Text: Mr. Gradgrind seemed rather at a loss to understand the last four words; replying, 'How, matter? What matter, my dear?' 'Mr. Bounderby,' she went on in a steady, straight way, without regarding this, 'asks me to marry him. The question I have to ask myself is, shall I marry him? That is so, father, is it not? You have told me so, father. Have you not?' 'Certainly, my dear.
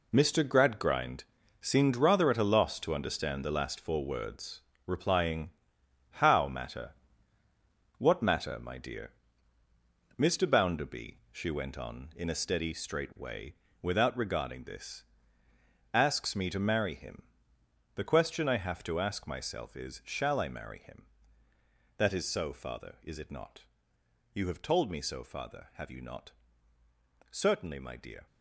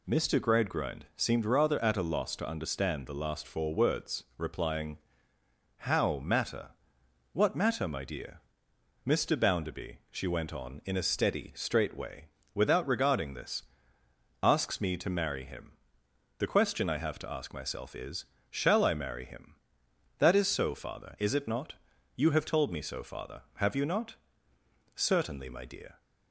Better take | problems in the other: second | gets quieter; strong; throughout; 10 dB // pauses between "Gradgrind" and "seemed"; at 1.2 s; 0.38 s long

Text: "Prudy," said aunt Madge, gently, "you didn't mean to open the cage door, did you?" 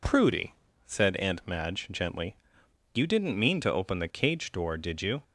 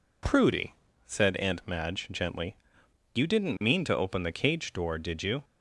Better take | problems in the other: neither | none

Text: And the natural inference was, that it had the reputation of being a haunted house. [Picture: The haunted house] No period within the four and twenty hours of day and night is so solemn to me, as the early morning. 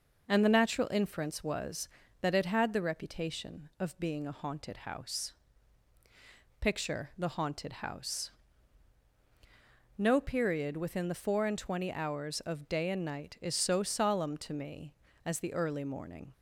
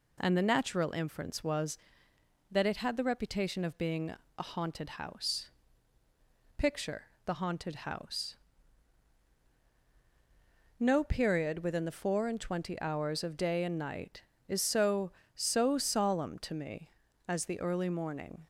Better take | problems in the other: first | pauses between "being" and "a"; slight; at 4.1 s; 0.28 s long // pauses between "house" and "No"; strong; at 8.3 s; 2.4 s long; strong in the first // says "so" twice; at 15.3 s

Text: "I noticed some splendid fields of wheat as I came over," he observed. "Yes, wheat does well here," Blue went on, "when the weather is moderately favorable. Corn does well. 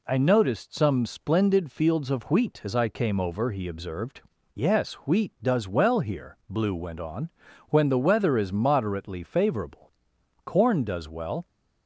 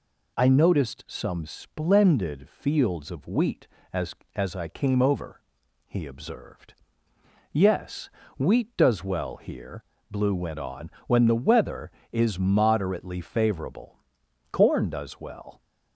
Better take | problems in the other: first | says "as" twice; at 4.3 s

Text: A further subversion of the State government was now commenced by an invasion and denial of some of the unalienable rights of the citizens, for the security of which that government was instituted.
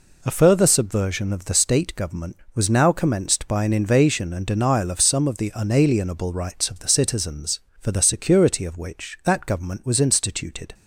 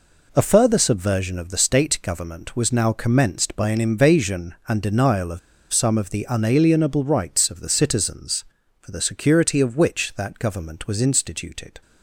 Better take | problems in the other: first | pauses between "of" and "some"; slight; at 5.3 s; 0.33 s long

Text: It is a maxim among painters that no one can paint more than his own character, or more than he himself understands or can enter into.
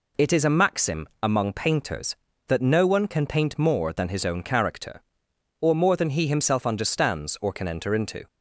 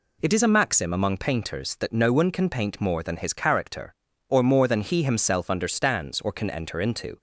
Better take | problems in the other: first | skips "own"; at 3.3 s

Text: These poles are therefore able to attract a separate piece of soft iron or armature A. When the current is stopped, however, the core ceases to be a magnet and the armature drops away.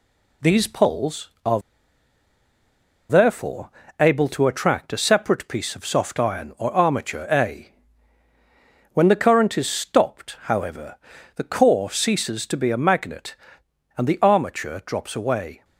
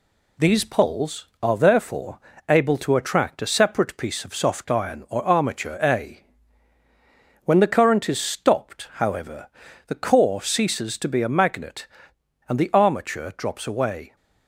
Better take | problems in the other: second | pauses between "are" and "therefore"; strong; at 1.5 s; 1.4 s long // pauses between "therefore" and "able"; slight; at 3.6 s; 0.30 s long; slight in the second

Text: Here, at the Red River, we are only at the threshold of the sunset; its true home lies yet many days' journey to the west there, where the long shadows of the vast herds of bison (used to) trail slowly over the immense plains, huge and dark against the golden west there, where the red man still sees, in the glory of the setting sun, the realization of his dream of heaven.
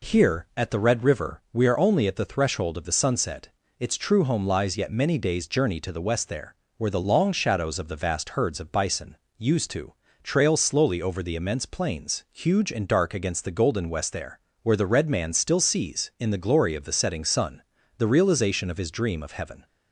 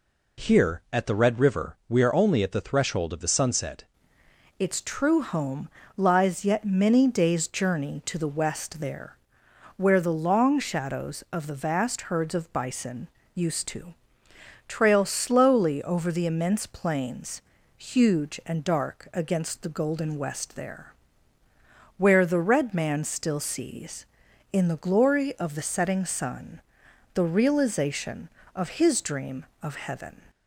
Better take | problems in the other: first | changes voice at "its"; from 4.5 s on; 25.7 s long // pauses between "home" and "lies"; slight; at 5.6 s; 0.30 s long

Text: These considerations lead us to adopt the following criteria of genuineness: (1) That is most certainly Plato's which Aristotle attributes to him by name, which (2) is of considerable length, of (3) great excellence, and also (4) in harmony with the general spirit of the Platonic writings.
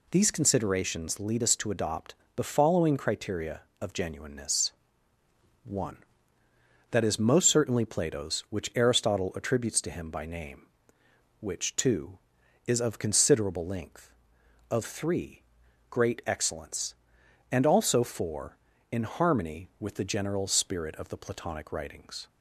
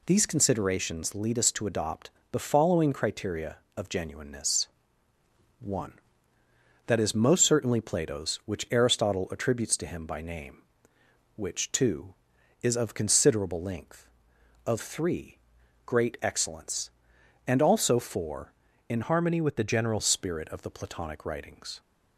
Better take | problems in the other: first | pauses between "adopt" and "the"; slight; at 2.1 s; 0.22 s long; slight in the first // changes voice from "harmony" to "general"; from 19.0 to 19.9 s; 0.9 s long

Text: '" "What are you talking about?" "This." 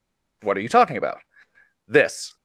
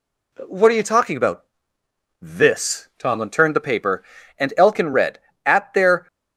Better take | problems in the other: first | goes on to say "Tomlin turned the paper and Elkin read At their"; strong; from 2.9 s on; 3.0 s long

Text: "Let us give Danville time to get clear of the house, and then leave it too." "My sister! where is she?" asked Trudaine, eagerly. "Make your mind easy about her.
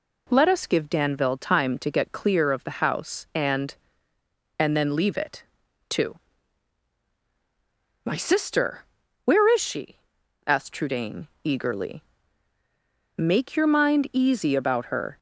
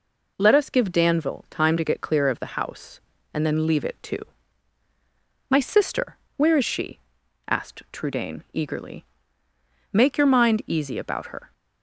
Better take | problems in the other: second | says "and" twice; at 4.5 s // pauses between "it" and "too"; at 5.4 s; 0.44 s long

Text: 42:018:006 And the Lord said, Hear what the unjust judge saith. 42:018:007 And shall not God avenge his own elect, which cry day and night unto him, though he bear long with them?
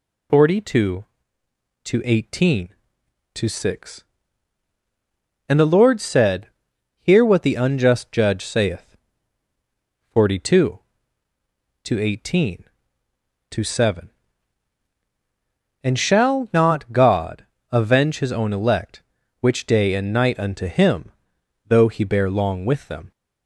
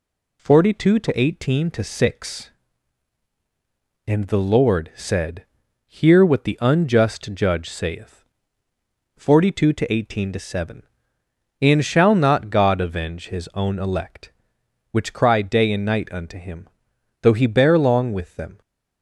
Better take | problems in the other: second | pauses between "God" and "avenge"; slight; at 17.4 s; 0.24 s long // skips "cry"; at 19.6 s

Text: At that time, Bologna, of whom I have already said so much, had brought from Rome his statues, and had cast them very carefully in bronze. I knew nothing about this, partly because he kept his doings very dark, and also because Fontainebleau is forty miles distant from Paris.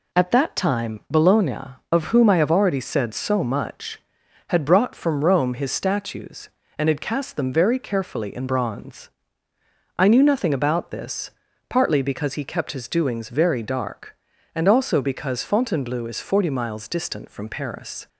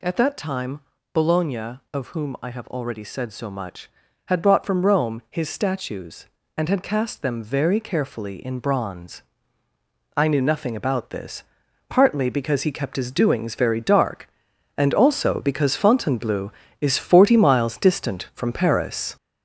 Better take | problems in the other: first | gets louder; noticeable; throughout; 5 dB

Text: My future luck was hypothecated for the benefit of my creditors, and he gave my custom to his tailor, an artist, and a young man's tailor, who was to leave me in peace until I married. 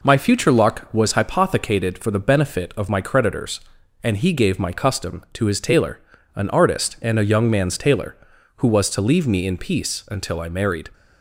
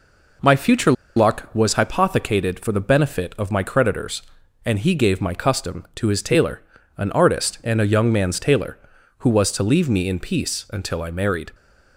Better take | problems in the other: first | pauses between "future" and "luck"; slight; at 0.9 s; 0.24 s long

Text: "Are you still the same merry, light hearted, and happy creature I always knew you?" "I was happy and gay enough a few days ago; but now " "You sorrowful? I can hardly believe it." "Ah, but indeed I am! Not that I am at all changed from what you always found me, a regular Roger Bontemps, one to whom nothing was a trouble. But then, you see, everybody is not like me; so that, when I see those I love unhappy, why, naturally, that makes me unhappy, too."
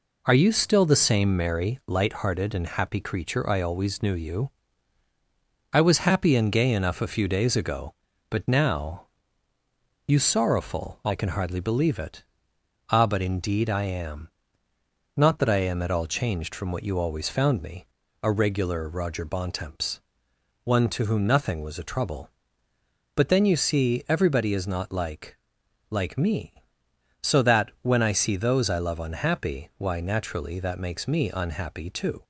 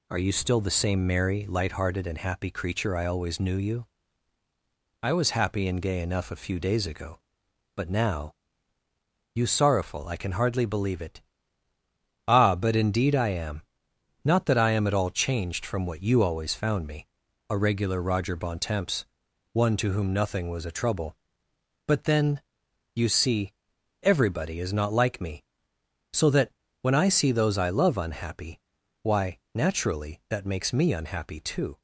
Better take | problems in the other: second | says "like" twice; at 25.8 s

